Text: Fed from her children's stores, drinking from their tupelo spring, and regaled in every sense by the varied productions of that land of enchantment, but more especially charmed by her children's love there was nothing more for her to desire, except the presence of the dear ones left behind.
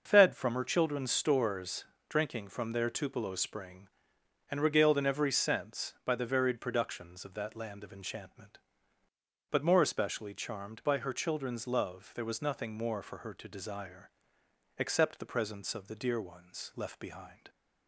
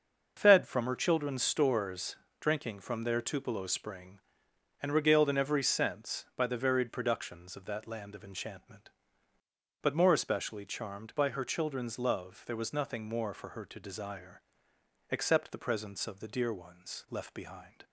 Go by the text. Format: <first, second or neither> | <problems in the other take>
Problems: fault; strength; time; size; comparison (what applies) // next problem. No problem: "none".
neither | starts louder than the rest; noticeable; the same in both